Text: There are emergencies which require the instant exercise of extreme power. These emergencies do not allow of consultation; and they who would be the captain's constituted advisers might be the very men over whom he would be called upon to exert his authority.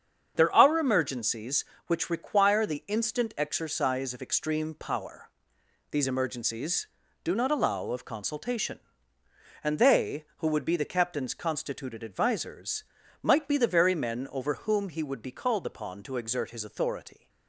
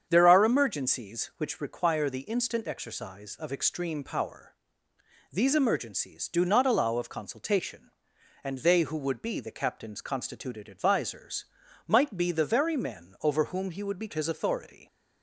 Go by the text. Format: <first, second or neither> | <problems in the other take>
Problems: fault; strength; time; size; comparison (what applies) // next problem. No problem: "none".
first | starts louder than the rest; strong; until 1.1 s; 7.5 dB; strong in the first // pauses between "advisers" and "might"; at 11.4 s; 0.42 s long; also in the first // skips "called upon to exert"; at 14.1 s